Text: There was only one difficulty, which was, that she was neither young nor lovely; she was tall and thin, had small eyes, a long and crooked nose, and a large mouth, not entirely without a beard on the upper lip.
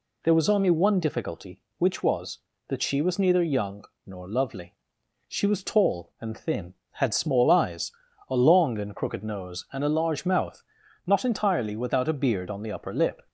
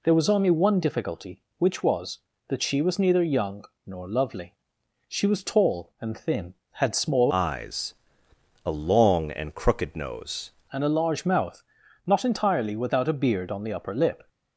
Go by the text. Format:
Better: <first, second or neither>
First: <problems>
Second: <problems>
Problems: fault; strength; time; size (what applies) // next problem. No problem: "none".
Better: first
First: pauses between "young" and "nor"; slight; at 3.8 s; 0.20 s long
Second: pauses between "young" and "nor"; slight; at 3.6 s; 0.20 s long // changes voice from "eyes" to "nose"; from 7.2 to 10.4 s; 3.2 s long